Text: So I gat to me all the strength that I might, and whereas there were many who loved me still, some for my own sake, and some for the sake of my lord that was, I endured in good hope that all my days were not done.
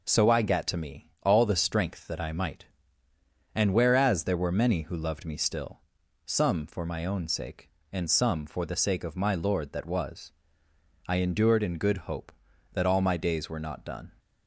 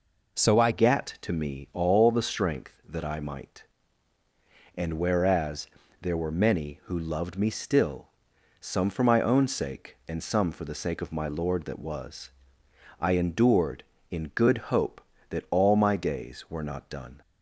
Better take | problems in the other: first | changes voice at "gat"; from 0.7 s on; 16.4 s long // pauses between "whereas" and "there"; slight; at 5.6 s; 0.34 s long // pauses between "good" and "hope"; slight; at 14.5 s; 0.16 s long

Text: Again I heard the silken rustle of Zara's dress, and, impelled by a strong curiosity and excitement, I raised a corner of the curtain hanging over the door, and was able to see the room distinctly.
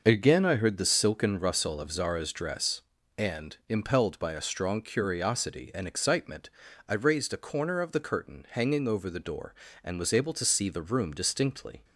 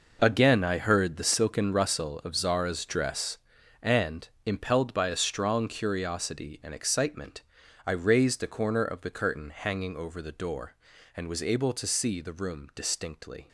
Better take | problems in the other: first | gets quieter; strong; throughout; 12 dB

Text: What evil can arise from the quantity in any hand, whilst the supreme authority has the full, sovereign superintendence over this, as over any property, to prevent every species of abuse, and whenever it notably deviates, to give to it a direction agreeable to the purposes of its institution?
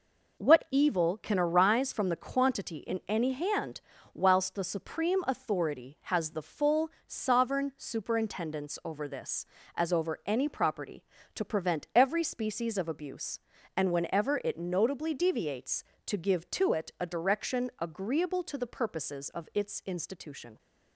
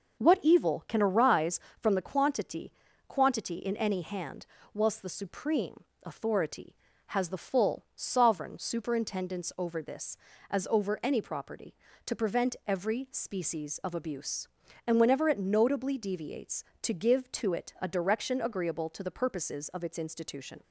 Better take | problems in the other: first | starts louder than the rest; until 1.2 s; 6 dB // says "quantity" twice; at 3.0 s // pauses between "supreme" and "authority"; slight; at 5.8 s; 0.18 s long

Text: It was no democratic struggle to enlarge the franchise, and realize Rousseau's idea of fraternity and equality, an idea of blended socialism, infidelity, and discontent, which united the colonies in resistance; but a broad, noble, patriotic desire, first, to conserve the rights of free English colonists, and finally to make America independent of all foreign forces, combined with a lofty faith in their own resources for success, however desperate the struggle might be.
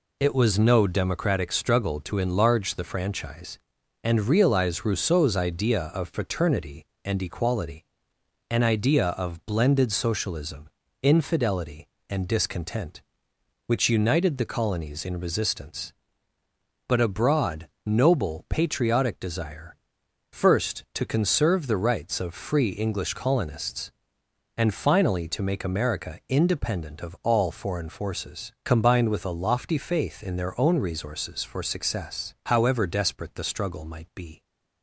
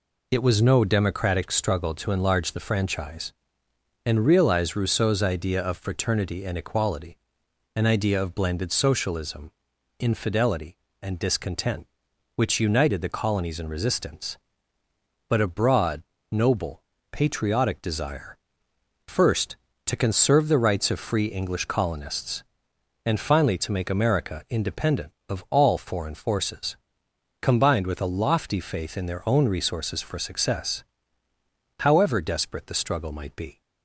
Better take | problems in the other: neither | none

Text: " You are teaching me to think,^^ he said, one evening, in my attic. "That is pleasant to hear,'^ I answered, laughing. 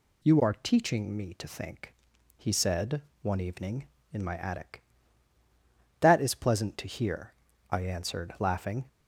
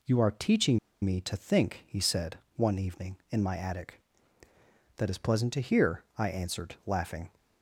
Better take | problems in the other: first | pauses between "teaching" and "me"; slight; at 0.7 s; 0.25 s long

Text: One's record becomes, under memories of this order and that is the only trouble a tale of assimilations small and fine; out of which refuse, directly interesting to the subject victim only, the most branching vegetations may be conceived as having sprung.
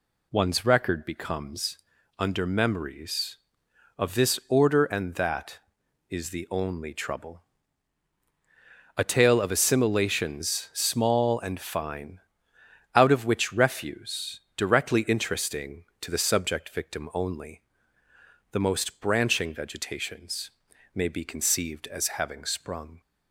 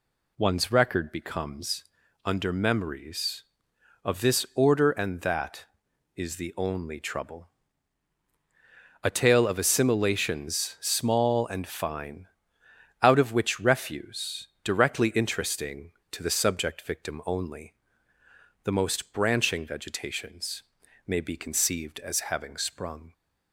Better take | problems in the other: neither | pauses between "trouble" and "a"; strong; the same in both // pauses between "vegetations" and "may"; the same in both

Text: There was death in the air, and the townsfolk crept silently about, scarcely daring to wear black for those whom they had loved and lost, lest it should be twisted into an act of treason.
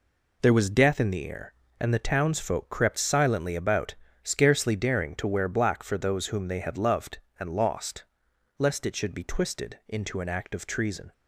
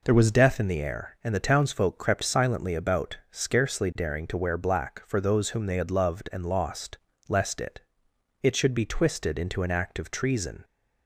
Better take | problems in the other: first | says "it" twice; at 8.4 s

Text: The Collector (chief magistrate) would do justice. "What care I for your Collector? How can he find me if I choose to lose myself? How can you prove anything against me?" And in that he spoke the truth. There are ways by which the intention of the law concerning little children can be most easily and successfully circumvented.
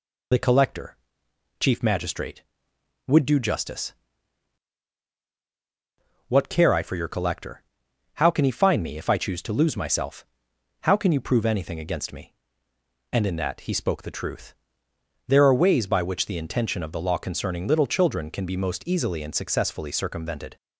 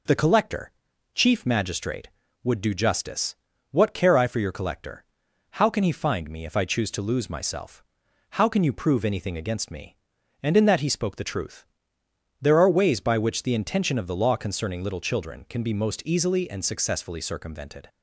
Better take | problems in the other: second | loses the start of "The"; at 0.3 s; 35 ms

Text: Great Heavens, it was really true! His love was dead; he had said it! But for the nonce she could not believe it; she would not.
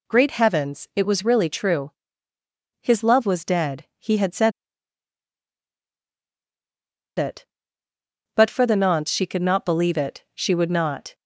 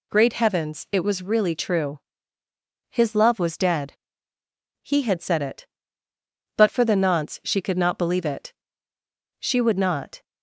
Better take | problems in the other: second | pauses between "said" and "it"; strong; at 4.5 s; 2.6 s long

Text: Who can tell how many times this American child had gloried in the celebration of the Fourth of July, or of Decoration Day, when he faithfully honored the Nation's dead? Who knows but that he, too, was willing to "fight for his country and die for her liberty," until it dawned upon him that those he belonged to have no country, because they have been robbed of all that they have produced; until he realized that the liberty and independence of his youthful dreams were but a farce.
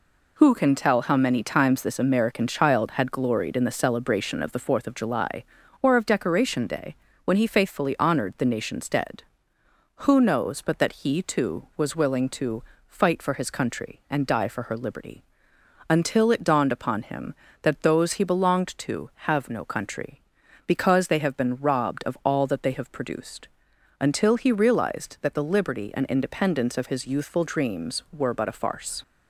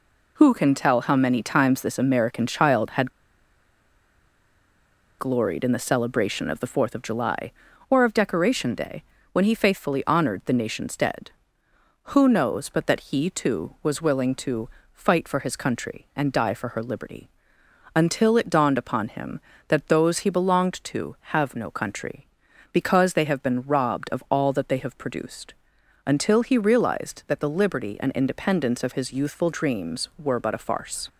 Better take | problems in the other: first | pauses between "had" and "gloried"; strong; at 3.1 s; 2.0 s long // pauses between "to" and "fight"; slight; at 14.6 s; 0.24 s long; slight in the first

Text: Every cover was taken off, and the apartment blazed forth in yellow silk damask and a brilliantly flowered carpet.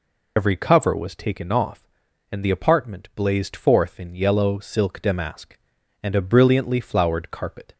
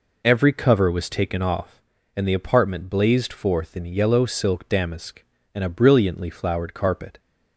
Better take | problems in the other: second | loses the start of "Every"; at 0.3 s; 60 ms

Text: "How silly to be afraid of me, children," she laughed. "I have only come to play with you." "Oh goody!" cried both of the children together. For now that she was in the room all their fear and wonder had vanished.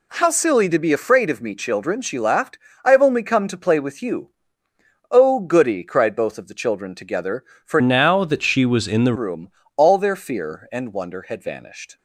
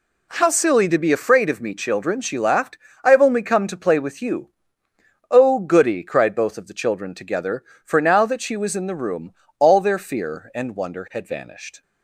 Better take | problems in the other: second | changes voice from "now" to "the"; from 7.7 to 9.1 s; 1.4 s long // pauses between "room" and "all"; slight; at 9.4 s; 0.26 s long; slight in the second

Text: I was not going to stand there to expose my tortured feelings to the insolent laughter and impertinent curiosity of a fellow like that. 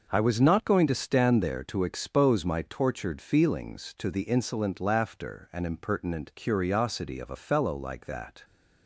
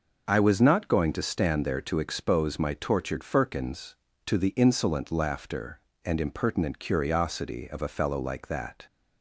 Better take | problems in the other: first | says "firkins" for "feelings"; at 3.2 s

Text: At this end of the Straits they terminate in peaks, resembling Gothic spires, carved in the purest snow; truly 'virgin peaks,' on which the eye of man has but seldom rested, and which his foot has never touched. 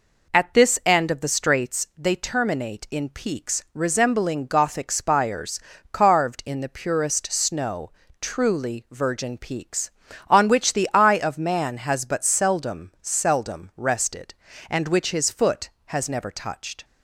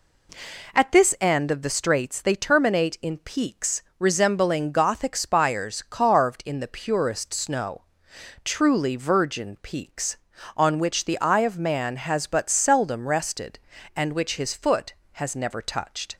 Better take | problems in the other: second | says "seldom" twice; at 13.0 s

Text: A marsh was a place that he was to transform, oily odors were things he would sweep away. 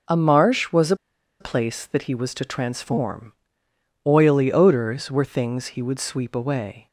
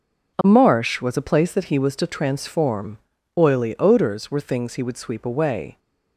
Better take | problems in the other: second | pauses between "a" and "place"; at 0.9 s; 0.44 s long

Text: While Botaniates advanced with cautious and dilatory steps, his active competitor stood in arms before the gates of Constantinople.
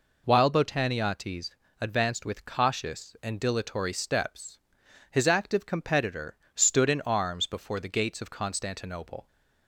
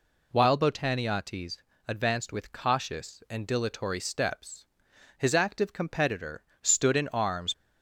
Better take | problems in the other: first | pauses between "Botaniates" and "advanced"; slight; at 1.5 s; 0.28 s long; slight in the first // pauses between "competitor" and "stood"; slight; at 6.4 s; 0.20 s long; slight in the first // stops before "before the gates of Constantinople"; at 7.5 s

